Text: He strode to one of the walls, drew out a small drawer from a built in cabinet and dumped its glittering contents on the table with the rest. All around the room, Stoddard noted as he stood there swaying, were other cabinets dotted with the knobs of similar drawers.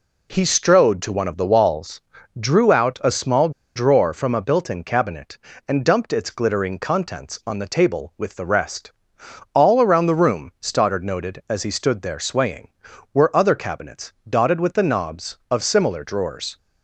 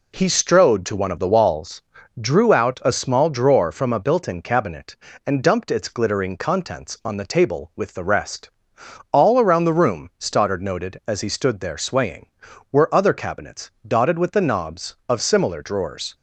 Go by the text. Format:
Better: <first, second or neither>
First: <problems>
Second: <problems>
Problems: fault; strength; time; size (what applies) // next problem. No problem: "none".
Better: second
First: pauses between "small" and "drawer"; slight; at 3.4 s; 0.25 s long // pauses between "cabinets" and "dotted"; slight; at 14.1 s; 0.16 s long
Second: pauses between "cabinets" and "dotted"; slight; at 13.7 s; 0.16 s long